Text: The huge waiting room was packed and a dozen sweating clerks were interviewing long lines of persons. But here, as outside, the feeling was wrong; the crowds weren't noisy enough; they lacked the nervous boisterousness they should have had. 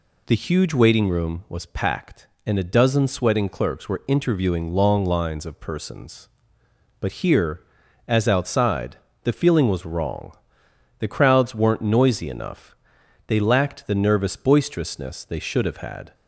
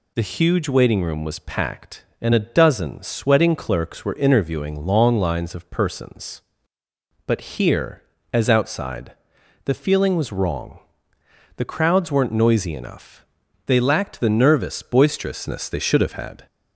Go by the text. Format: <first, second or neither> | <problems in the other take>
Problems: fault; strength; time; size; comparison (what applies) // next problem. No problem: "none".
neither | none